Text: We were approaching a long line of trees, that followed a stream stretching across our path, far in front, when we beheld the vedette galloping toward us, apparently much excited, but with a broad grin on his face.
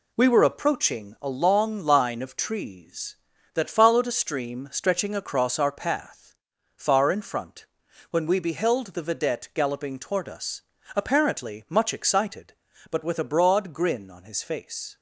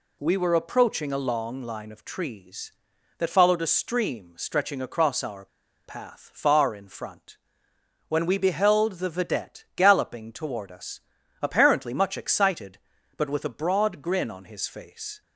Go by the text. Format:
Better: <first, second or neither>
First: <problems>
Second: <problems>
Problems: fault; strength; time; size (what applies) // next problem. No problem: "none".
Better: first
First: none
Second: pauses between "our" and "path"; at 5.4 s; 0.40 s long